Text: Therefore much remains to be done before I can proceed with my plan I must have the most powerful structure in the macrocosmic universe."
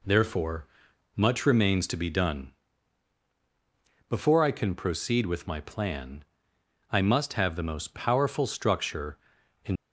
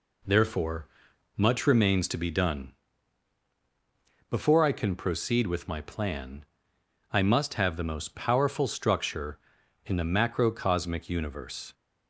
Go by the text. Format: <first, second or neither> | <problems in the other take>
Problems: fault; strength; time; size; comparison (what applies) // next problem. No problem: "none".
second | pauses between "Therefore" and "much"; noticeable; at 0.6 s; 0.48 s long; noticeable in the second // pauses between "done" and "before"; strong; at 2.5 s; 1.5 s long; strong in the second // pauses between "plan" and "I"; noticeable; at 6.2 s; 0.68 s long; noticeable in the second // stops before "the macrocosmic universe"; at 9.7 s